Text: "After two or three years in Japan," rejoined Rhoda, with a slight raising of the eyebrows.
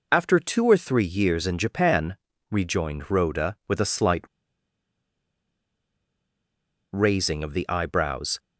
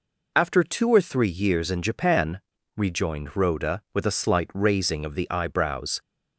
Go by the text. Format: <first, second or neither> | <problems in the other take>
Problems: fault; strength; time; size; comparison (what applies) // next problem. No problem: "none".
second | pauses between "slight" and "raising"; strong; at 4.2 s; 2.6 s long